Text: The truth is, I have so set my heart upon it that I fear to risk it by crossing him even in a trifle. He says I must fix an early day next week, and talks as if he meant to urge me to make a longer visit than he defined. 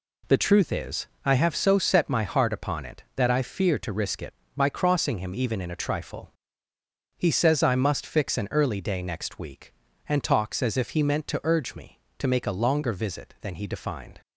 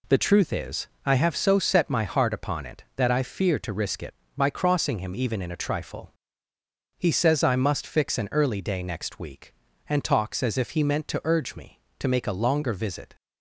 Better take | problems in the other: first | stops before "than he defined"; at 13.1 s

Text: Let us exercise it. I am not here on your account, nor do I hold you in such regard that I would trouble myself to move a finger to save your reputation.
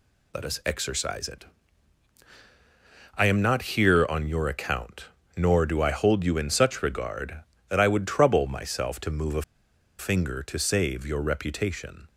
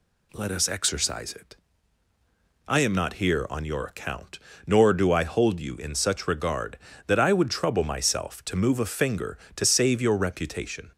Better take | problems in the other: second | pauses between "a" and "finger"; noticeable; at 9.4 s; 0.57 s long

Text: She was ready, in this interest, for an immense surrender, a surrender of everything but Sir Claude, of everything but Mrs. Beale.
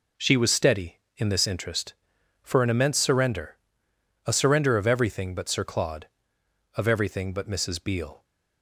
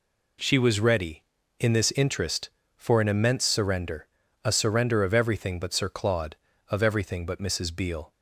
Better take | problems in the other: second | says "steady" for "ready"; at 0.5 s

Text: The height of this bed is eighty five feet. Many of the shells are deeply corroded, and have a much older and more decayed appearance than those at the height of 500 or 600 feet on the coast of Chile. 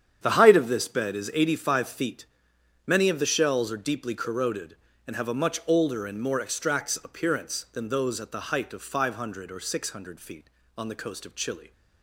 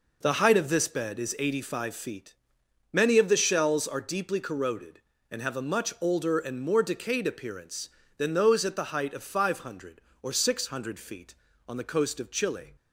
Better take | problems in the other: second | starts louder than the rest; strong; until 1.2 s; 8.5 dB // says "extracts" for "decayed"; at 6.4 s

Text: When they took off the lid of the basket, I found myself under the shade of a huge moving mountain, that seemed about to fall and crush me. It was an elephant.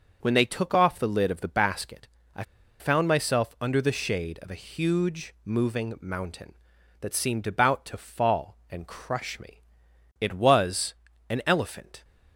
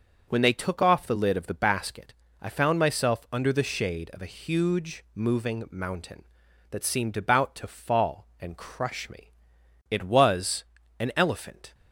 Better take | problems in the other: second | starts louder than the rest; noticeable; until 1.2 s; 6 dB; noticeable in the second // pauses between "I" and "found"; at 2.4 s; 0.36 s long // pauses between "was" and "an"; slight; at 10.9 s; 0.34 s long; slight in the second

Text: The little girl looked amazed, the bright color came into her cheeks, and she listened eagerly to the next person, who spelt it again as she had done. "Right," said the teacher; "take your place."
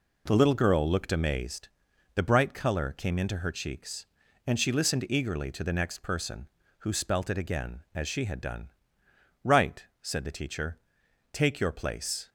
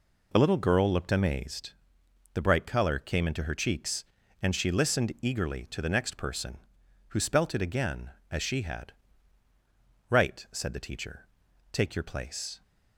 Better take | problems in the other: first | skips "done"; at 9.5 s

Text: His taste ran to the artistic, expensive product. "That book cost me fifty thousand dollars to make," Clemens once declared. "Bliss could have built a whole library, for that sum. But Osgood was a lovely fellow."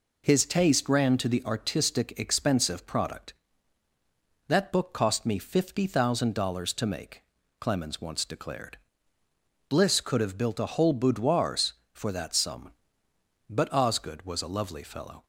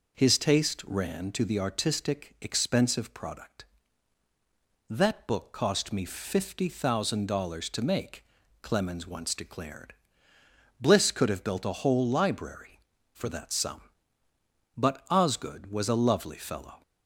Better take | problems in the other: second | says "boudoirs" for "library"; at 10.9 s

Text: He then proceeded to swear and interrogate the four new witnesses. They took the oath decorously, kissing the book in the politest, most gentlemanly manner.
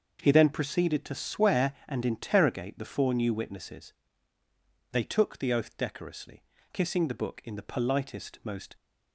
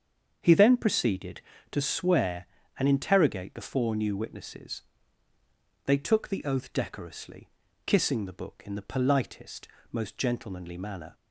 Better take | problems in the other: second | starts louder than the rest; until 1.2 s; 6.5 dB; strong in the second // stops before "gentlemanly manner"; at 8.7 s

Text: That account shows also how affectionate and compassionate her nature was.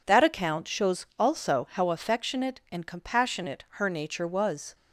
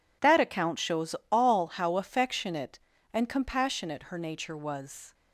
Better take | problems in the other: first | says "all" for "also"; at 1.3 s

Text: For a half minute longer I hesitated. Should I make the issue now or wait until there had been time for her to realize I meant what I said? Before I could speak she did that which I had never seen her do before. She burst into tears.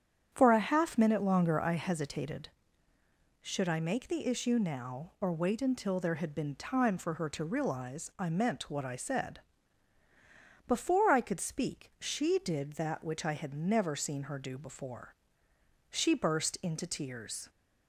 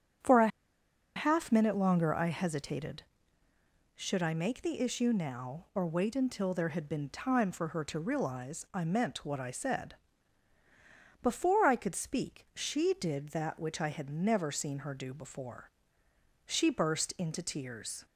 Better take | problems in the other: first | starts louder than the rest; strong; until 1.9 s; 8.5 dB; strong in the first // pauses between "a" and "half"; noticeable; at 0.4 s; 0.68 s long

